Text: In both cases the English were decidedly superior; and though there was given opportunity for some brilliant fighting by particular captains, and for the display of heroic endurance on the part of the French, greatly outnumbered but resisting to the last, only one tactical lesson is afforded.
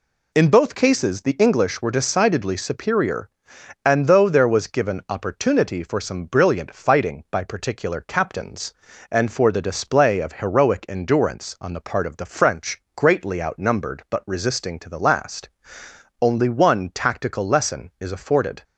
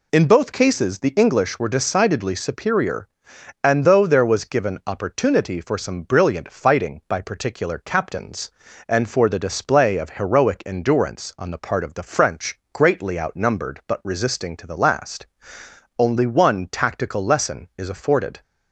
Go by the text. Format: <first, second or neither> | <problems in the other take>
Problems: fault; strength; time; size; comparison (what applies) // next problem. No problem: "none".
neither | none